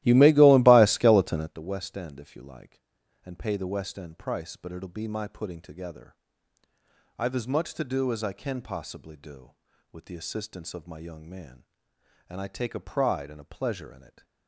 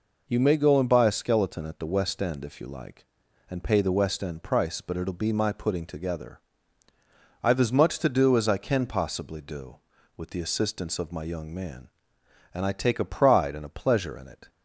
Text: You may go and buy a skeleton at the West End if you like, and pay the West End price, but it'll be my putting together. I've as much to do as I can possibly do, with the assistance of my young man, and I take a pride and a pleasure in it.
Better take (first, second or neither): second